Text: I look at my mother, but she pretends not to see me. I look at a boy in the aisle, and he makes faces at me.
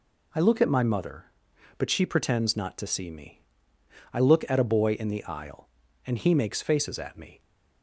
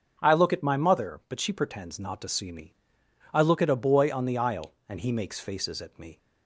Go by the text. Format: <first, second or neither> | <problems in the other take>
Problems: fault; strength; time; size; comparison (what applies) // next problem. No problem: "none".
first | starts louder than the rest; until 1.2 s; 6.5 dB // says "on" for "in"; at 4.1 s